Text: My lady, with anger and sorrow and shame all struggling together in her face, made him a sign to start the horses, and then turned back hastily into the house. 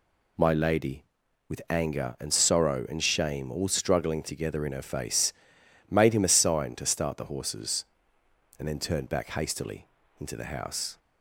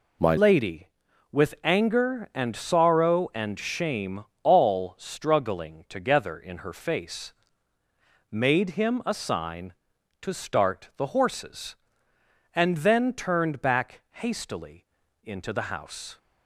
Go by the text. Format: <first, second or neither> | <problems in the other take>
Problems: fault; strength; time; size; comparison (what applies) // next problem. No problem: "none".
first | changes voice at "lady"; from 0.3 s on; 15.8 s long // pauses between "shame" and "all"; slight; at 4.2 s; 0.18 s long // pauses between "hastily" and "into"; at 14.8 s; 0.40 s long; slight in the first